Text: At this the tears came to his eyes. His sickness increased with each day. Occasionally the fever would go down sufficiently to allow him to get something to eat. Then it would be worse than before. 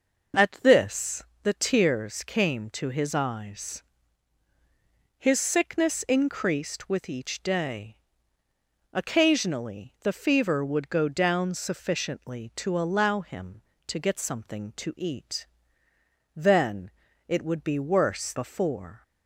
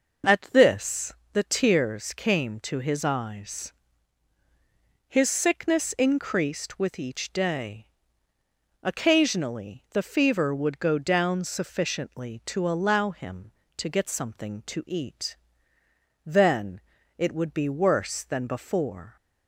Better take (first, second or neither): second